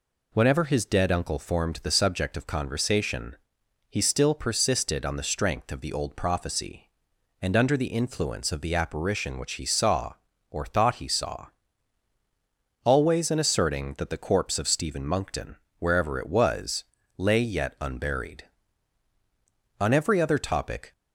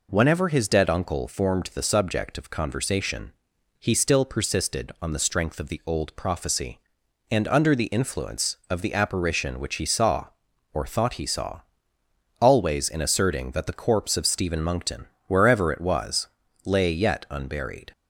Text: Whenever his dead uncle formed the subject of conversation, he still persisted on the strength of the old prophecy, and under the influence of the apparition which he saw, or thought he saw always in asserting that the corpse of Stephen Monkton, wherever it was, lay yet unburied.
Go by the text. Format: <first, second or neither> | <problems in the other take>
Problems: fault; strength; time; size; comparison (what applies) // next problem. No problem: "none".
second | pauses between "saw" and "always"; strong; at 11.4 s; 1.3 s long; noticeable in the second // goes on to say "On every other topic"; noticeable; from 19.7 s on; 1.1 s long